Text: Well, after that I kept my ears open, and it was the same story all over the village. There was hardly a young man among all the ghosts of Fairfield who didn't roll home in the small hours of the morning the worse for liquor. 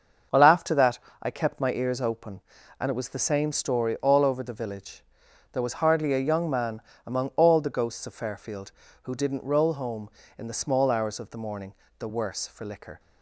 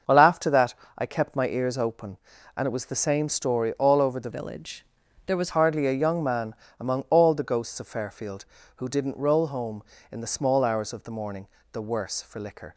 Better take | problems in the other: first | starts louder than the rest; until 1.2 s; 6.5 dB; also in the first // pauses between "that" and "I"; slight; at 0.7 s; 0.22 s long; slight in the first // changes voice from "village" to "was"; from 4.3 to 5.4 s; 1.1 s long // pauses between "man" and "among"; slight; at 6.5 s; 0.24 s long; slight in the first // pauses between "morning" and "the"; slight; at 11.4 s; 0.26 s long; slight in the first

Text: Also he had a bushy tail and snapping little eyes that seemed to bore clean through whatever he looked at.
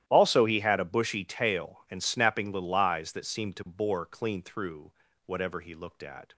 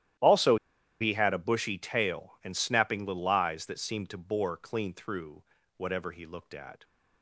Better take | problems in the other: first | starts louder than the rest; strong; until 1.6 s; 12.5 dB; strong in the first // pauses between "Also" and "he"; at 0.5 s; 0.45 s long // pauses between "through" and "whatever"; slight; at 5.4 s; 0.36 s long; slight in the first

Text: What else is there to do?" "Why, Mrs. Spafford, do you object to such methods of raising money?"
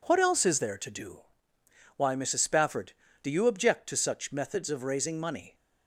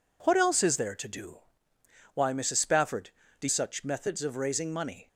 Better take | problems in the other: first | skips "you object to"; at 3.4 s

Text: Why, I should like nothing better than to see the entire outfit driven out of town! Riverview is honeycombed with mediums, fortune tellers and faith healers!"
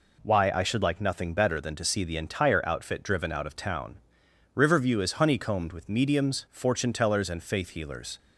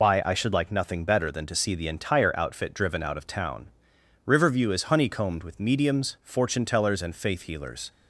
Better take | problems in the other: first | loses the start of "Why"; at 0.0 s; 110 ms

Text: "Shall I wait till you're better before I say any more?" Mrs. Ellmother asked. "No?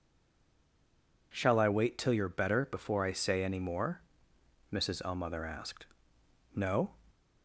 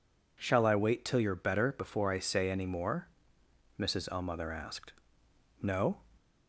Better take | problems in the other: second | stays silent before the first word; noticeable; until 1.3 s; 1.3 s long

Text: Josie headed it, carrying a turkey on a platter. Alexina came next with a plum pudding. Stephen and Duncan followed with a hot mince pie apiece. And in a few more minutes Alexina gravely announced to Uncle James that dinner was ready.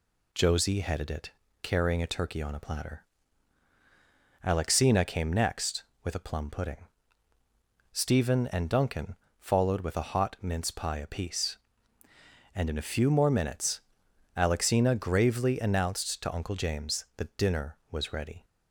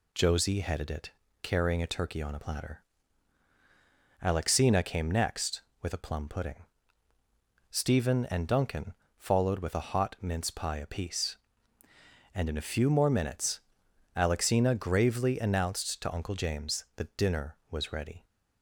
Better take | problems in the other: neither | pauses between "Duncan" and "followed"; slight; the same in both // pauses between "minutes" and "Alexina"; noticeable; the same in both

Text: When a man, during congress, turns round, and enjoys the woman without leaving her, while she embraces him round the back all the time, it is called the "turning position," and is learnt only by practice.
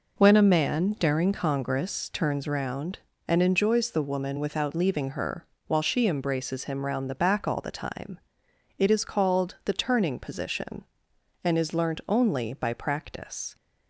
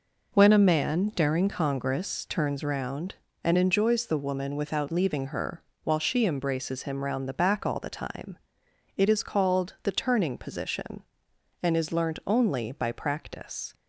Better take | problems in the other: neither | none

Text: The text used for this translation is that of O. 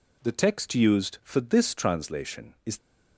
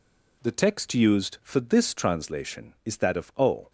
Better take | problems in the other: second | stops before "that of O"; at 2.7 s

